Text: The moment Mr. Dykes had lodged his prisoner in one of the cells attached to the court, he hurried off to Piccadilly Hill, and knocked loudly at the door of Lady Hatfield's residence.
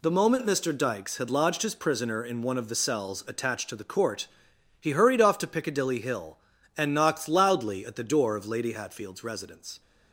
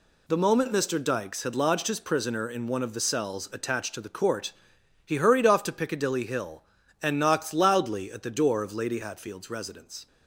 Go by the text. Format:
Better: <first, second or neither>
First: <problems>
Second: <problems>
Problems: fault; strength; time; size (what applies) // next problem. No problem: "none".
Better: neither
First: none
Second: none